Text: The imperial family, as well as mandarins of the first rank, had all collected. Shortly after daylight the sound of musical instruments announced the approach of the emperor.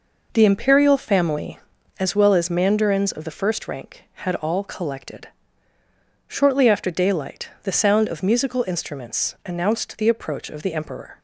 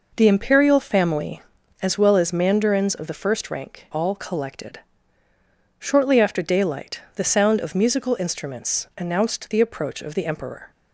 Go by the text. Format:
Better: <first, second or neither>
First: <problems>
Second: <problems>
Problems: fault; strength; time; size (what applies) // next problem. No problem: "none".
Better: first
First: pauses between "daylight" and "the"; slight; at 7.4 s; 0.15 s long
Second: skips "had"; at 3.8 s // pauses between "daylight" and "the"; slight; at 7.0 s; 0.16 s long